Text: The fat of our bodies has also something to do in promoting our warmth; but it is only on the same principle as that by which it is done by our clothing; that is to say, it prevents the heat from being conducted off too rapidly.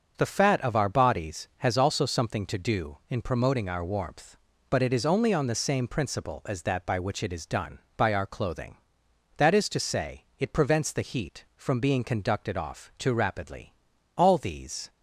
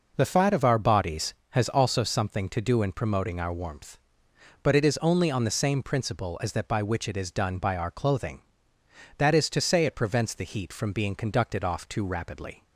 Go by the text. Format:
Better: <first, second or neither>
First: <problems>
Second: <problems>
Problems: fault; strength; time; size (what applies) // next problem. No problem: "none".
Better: second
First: goes on to say "All these"; noticeable; from 14.1 s on; 0.72 s long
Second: none